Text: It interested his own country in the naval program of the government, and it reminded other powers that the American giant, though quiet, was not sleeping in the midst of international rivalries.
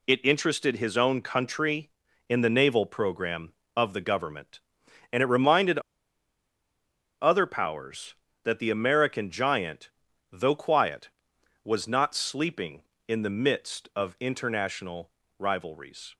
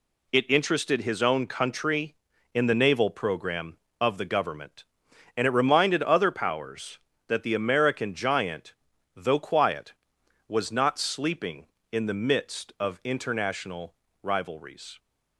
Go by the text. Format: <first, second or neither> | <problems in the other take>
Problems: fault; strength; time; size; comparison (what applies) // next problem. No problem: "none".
second | pauses between "reminded" and "other"; strong; at 5.7 s; 1.4 s long // pauses between "international" and "rivalries"; slight; at 15.1 s; 0.28 s long; slight in the second